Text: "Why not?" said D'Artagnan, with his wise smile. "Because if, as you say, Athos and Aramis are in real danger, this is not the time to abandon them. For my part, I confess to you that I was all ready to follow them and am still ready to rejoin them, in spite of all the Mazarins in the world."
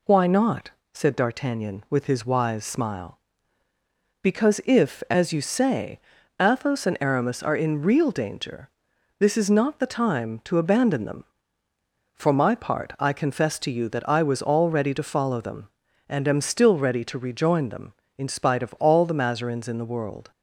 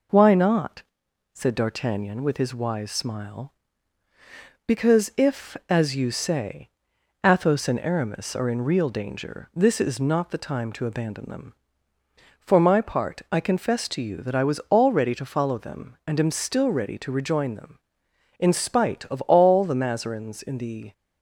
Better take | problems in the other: first | stops before "world"; at 20.9 s

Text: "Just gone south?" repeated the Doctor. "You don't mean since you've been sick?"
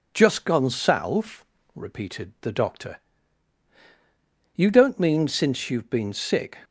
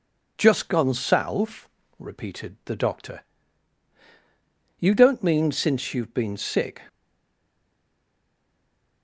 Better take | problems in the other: first | stays silent after the last word; from 6.8 s on; 2.2 s long

